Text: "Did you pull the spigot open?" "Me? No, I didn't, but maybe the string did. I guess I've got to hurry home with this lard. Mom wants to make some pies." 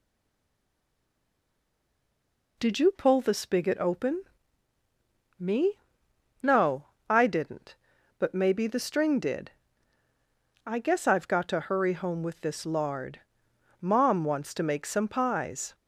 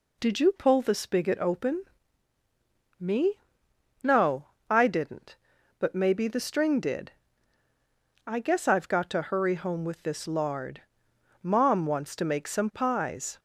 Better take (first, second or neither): second